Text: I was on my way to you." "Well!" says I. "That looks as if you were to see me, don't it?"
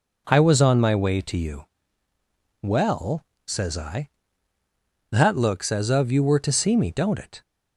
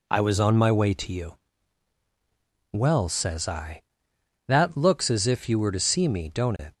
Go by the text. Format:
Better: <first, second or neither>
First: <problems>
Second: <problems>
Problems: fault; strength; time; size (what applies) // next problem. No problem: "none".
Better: second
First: says "of" for "if"; at 5.8 s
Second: none